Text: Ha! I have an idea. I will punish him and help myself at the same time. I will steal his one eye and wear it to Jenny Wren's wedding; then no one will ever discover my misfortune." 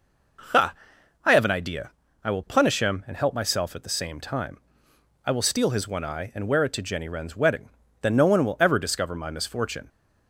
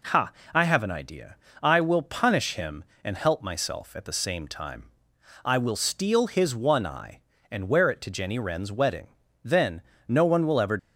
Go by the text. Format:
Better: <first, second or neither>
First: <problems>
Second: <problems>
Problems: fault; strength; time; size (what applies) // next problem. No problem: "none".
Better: first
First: none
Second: pauses between "then" and "no"; slight; at 9.8 s; 0.26 s long // stops before "discover my misfortune"; at 10.7 s